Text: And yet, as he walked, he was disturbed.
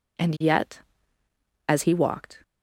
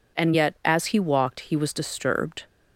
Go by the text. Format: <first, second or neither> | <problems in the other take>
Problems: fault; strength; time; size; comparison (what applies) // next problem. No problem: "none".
second | stops before "he was disturbed"; at 2.4 s